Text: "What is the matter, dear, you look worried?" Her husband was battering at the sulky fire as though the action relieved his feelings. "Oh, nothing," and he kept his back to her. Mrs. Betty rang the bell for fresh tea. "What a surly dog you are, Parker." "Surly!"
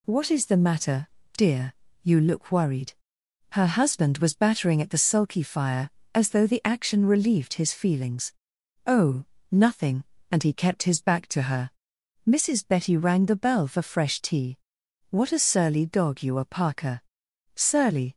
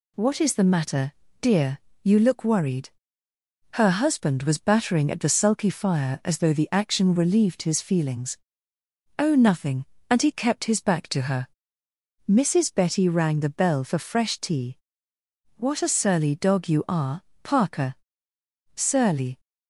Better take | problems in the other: neither | none

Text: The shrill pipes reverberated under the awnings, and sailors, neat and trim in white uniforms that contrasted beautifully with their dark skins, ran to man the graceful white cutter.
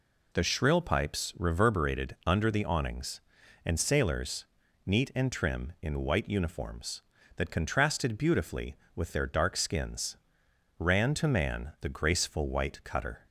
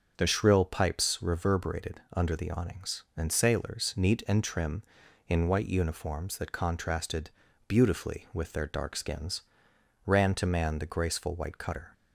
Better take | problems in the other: first | starts louder than the rest; until 1.1 s; 6.5 dB // changes voice at "shrill"; from 0.2 s on; 11.7 s long // pauses between "reverberated" and "under"; slight; at 1.9 s; 0.16 s long // pauses between "contrasted" and "beautifully"; at 7.2 s; 0.38 s long

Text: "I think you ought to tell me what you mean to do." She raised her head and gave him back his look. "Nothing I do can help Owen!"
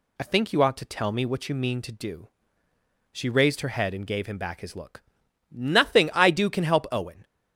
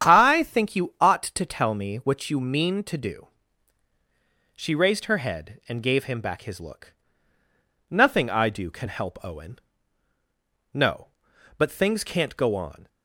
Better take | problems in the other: first | starts louder than the rest; strong; until 1.1 s; 9 dB // goes on to say "No but things can't go on"; strong; from 10.7 s on; 2.1 s long

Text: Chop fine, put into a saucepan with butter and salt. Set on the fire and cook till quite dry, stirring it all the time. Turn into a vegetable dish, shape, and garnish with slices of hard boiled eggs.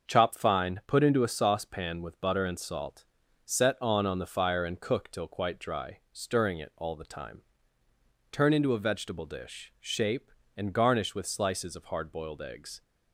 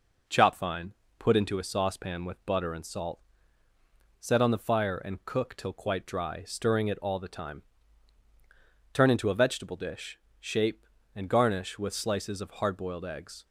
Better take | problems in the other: second | starts louder than the rest; until 1.1 s; 6.5 dB // says "on" twice; at 4.0 s

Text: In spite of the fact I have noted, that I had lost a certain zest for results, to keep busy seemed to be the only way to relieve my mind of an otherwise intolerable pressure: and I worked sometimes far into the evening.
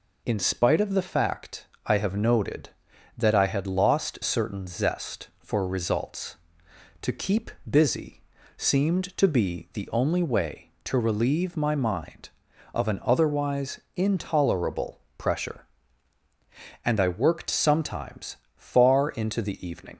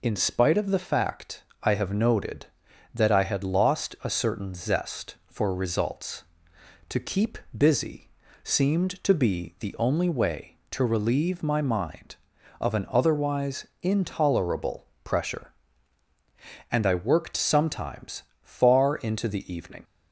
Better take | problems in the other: second | pauses between "fact" and "I"; slight; at 1.6 s; 0.20 s long; slight in the second // skips "a"; at 4.1 s // pauses between "keep" and "busy"; slight; at 7.4 s; 0.18 s long; slight in the second // pauses between "busy" and "seemed"; slight; at 8.2 s; 0.34 s long; slight in the second // pauses between "otherwise" and "intolerable"; slight; at 13.7 s; 0.16 s long; slight in the second // pauses between "intolerable" and "pressure"; slight; at 14.9 s; 0.18 s long; slight in the second // pauses between "sometimes" and "far"; slight; at 18.3 s; 0.20 s long; slight in the second

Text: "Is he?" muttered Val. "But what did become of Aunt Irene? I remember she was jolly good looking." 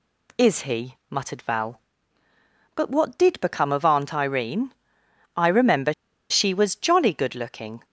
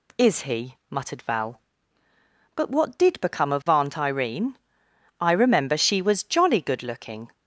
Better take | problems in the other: second | pauses between "remember" and "she"; at 5.9 s; 0.37 s long

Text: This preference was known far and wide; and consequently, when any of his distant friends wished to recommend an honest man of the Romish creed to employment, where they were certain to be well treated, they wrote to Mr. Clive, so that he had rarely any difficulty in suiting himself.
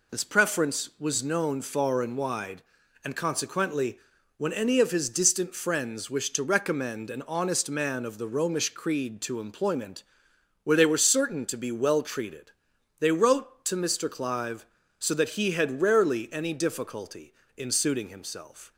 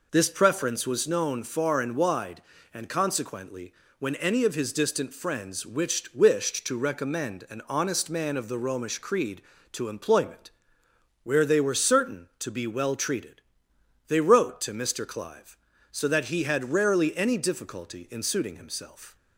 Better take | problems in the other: first | says "wished" twice; at 6.1 s

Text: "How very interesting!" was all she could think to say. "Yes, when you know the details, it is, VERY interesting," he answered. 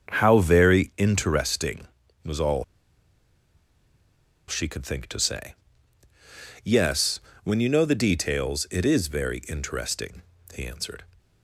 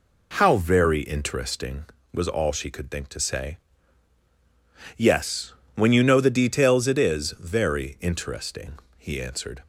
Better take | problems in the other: second | starts louder than the rest; until 1.1 s; 7 dB // pauses between "all" and "she"; strong; at 2.6 s; 1.8 s long

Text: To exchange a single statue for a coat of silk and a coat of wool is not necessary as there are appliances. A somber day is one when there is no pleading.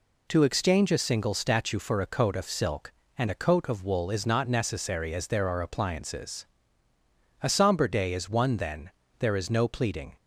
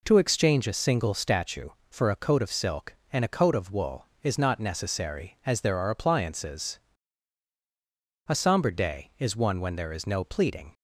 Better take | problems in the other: second | says "then" for "when"; at 8.5 s

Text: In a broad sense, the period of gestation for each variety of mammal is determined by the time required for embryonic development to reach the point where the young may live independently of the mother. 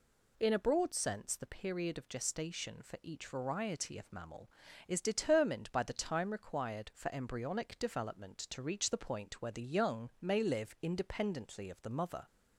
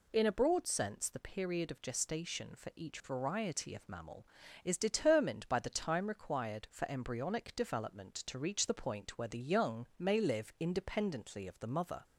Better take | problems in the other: neither | none

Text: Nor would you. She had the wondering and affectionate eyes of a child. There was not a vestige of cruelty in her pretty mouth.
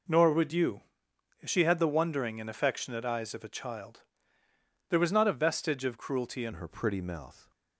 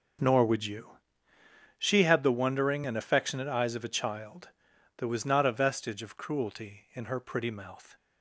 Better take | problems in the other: second | changes voice at "her"; from 6.5 s on; 1.0 s long

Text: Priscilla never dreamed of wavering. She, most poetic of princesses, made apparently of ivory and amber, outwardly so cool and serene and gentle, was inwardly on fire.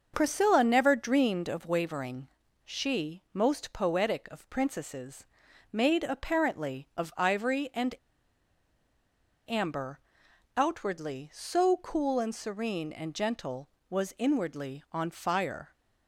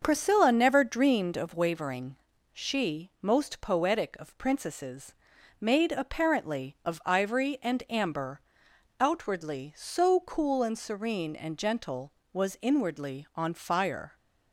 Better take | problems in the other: second | starts louder than the rest; until 1.1 s; 6.5 dB; also in the second // pauses between "and" and "amber"; strong; at 7.9 s; 1.5 s long

